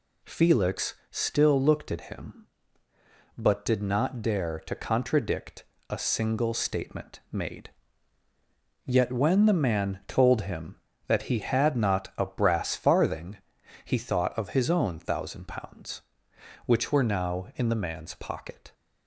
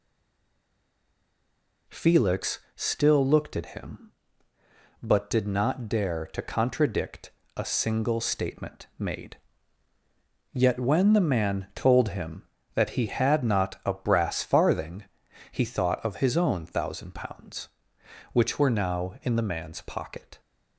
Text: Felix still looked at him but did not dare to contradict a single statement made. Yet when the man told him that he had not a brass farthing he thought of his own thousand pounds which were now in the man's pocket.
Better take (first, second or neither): first